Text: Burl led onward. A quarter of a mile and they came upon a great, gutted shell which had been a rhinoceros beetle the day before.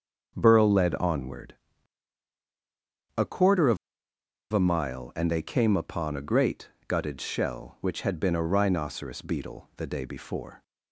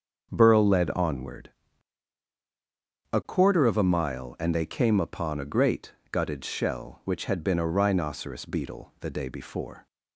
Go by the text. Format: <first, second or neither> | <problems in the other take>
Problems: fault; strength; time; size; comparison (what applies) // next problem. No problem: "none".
second | starts louder than the rest; until 1.3 s; 7 dB; also in the second // pauses between "of" and "a"; noticeable; at 3.7 s; 0.75 s long